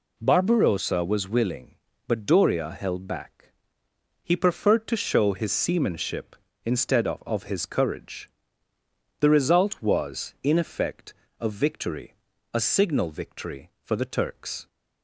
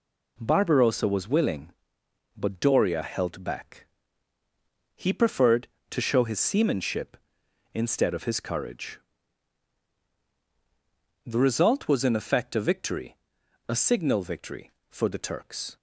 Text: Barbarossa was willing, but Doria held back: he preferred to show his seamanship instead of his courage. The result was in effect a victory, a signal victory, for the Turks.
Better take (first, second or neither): second